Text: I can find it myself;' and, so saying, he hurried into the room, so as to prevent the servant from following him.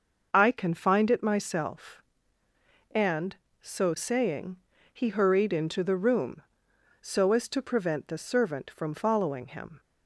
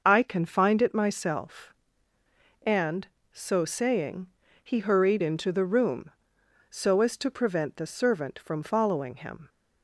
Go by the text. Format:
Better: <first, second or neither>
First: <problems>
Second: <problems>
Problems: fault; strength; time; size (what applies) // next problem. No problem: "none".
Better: neither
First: starts louder than the rest; noticeable; until 1.3 s; 6 dB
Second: starts louder than the rest; noticeable; until 1.0 s; 6 dB